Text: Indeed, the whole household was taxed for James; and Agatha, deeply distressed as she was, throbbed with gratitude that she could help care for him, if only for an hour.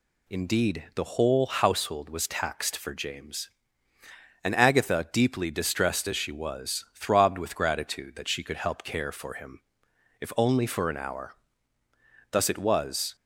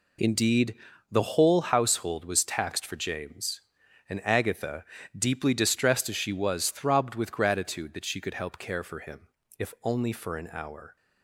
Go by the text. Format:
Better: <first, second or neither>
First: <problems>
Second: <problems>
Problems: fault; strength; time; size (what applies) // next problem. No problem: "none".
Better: second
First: goes on to say "Thus it was"; noticeable; from 12.3 s on; 0.84 s long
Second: none